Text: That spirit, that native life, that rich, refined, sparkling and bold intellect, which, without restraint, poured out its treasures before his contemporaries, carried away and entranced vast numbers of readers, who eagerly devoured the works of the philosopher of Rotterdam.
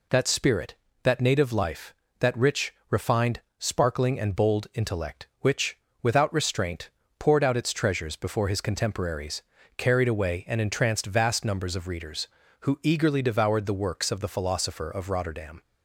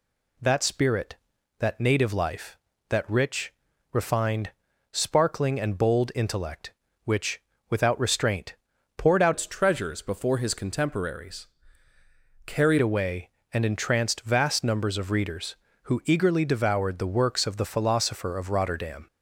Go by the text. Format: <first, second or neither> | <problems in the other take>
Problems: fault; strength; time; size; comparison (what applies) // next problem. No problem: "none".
first | changes voice from "its" to "carried"; from 9.3 to 12.7 s; 3.4 s long